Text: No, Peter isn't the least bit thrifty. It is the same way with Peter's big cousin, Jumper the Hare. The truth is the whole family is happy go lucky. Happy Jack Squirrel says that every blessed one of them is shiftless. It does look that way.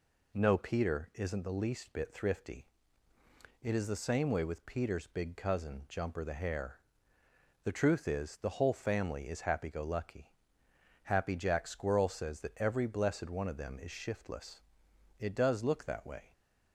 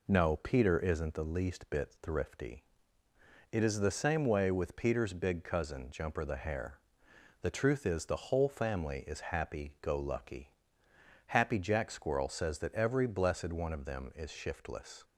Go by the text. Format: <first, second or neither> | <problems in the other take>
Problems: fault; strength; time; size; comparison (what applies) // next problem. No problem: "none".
first | stops before "It does look that way"; at 15.0 s